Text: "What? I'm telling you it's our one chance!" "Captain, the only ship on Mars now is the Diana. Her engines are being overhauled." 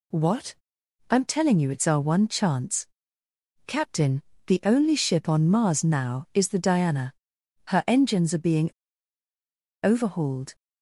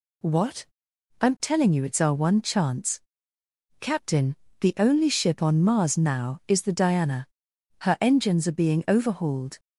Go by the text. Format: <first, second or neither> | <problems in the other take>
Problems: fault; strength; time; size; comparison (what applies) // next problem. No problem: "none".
second | pauses between "being" and "overhauled"; at 8.6 s; 1.1 s long